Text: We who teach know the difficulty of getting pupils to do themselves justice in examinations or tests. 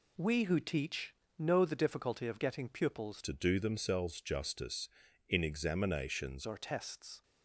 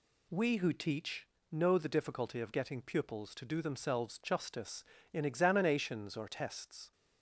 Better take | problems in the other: second | pauses between "teach" and "know"; slight; at 1.1 s; 0.28 s long; slight in the second // changes voice from "to" to "examinations"; from 3.2 to 6.4 s; 3.2 s long

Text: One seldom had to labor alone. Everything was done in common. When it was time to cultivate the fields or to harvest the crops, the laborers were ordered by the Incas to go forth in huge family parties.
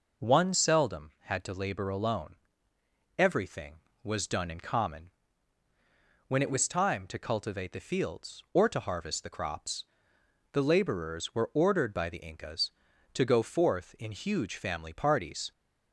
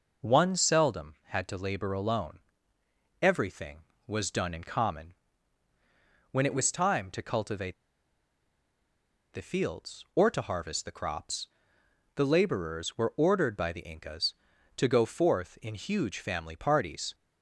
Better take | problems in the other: first | pauses between "cultivate" and "the"; strong; at 7.7 s; 1.5 s long

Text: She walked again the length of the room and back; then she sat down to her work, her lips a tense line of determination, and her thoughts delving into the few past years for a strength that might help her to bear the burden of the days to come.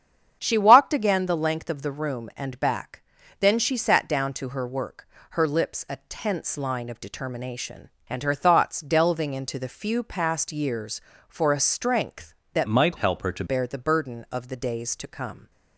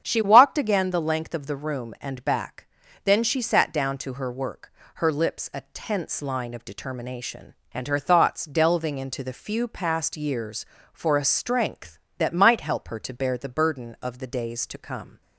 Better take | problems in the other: second | starts louder than the rest; strong; until 1.4 s; 8 dB; strong in the second // changes voice from "might" to "to"; from 12.6 to 13.4 s; 0.8 s long

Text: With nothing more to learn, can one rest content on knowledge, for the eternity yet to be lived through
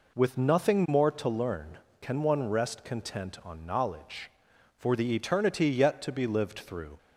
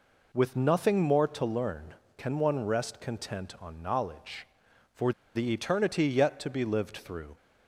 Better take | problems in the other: first | pauses between "for" and "the"; slight; at 5.1 s; 0.23 s long

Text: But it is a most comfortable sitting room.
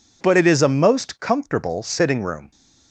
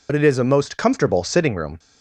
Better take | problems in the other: first | loses the start of "But"; at 0.0 s; 50 ms

